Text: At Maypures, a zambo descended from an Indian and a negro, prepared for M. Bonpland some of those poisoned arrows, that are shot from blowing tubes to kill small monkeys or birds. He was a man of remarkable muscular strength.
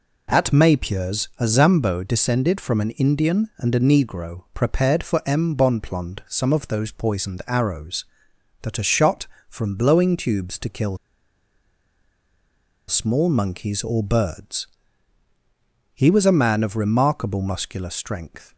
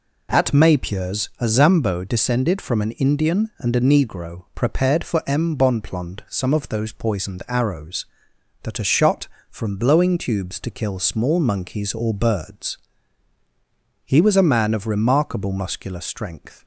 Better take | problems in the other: second | pauses between "kill" and "small"; strong; at 10.9 s; 1.9 s long

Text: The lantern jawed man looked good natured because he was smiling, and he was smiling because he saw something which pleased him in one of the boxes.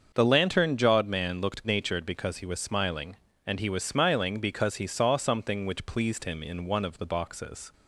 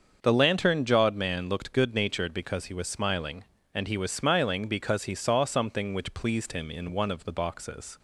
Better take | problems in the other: second | starts louder than the rest; until 1.1 s; 6.5 dB; also in the second // skips "good"; at 1.6 s

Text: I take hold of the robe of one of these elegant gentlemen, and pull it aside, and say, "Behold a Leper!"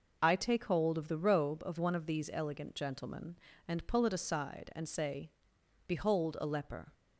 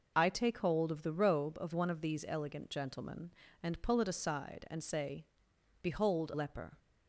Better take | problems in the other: first | skips "a"; at 6.3 s

